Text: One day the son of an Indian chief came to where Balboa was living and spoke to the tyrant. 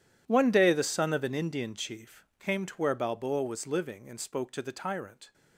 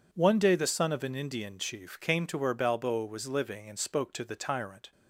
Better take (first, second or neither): second